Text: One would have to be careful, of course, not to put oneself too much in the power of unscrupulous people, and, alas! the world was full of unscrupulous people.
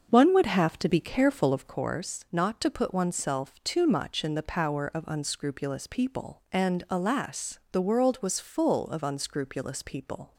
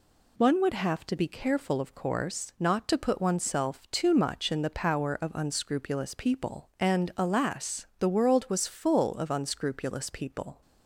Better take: second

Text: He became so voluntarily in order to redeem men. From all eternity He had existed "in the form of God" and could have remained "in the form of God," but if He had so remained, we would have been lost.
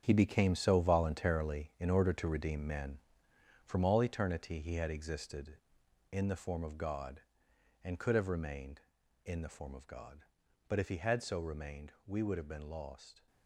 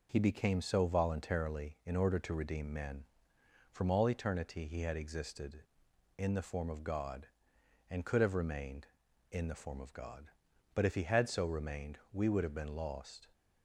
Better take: second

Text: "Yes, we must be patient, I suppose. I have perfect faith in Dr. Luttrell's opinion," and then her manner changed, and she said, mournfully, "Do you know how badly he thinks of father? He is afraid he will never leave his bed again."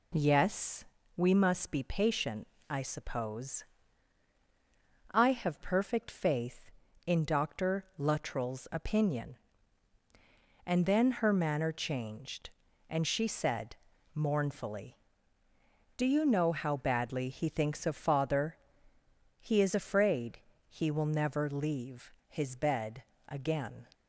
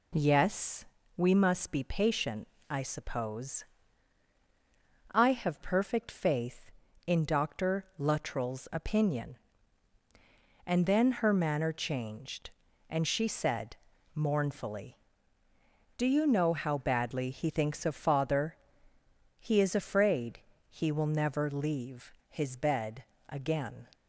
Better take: neither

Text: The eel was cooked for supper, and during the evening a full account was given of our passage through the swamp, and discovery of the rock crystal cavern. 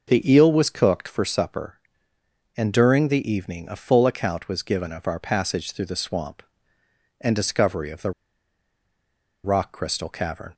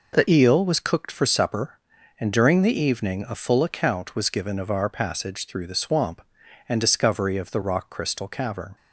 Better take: second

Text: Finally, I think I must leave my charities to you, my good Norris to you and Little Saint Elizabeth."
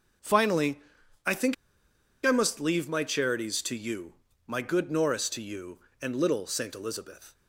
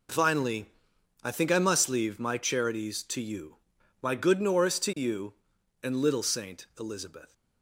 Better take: second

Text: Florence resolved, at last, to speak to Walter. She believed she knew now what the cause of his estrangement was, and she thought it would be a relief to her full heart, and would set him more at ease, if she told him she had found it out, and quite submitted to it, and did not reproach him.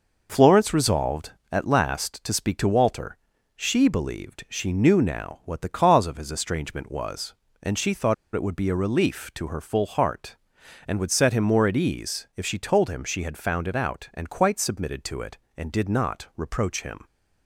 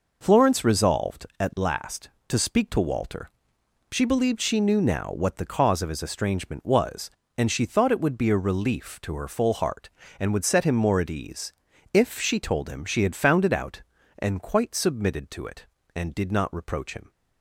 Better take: second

